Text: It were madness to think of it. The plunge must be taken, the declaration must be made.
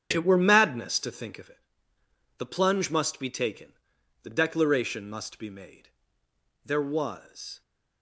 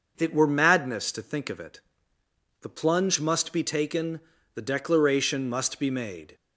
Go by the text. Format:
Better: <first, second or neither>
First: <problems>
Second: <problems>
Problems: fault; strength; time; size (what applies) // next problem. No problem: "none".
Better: second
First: starts louder than the rest; strong; until 1.1 s; 9 dB // goes on to say "There was"; noticeable; from 6.6 s on; 0.96 s long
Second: none